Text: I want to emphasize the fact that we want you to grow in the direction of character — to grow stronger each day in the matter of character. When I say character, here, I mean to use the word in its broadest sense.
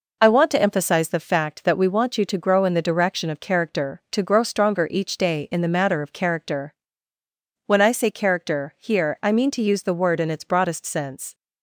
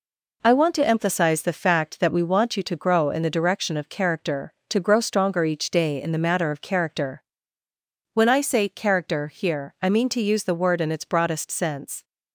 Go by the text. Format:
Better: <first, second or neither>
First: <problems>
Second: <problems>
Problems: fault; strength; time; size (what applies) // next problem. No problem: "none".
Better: neither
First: none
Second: none